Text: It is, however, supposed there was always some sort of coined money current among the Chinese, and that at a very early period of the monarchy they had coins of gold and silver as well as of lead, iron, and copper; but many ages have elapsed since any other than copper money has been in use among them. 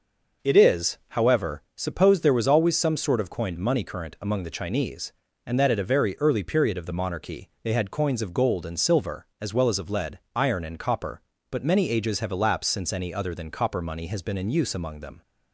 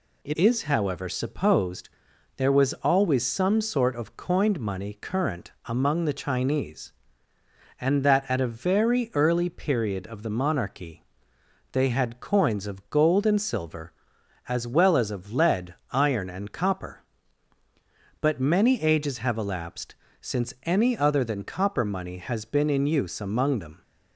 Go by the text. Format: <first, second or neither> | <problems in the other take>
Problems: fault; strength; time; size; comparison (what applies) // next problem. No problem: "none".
first | changes voice at "is"; from 0.3 s on; 23.5 s long // pauses between "supposed" and "there"; noticeable; at 1.8 s; 0.46 s long // pauses between "monarchy" and "they"; noticeable; at 11.0 s; 0.66 s long // pauses between "elapsed" and "since"; slight; at 19.9 s; 0.26 s long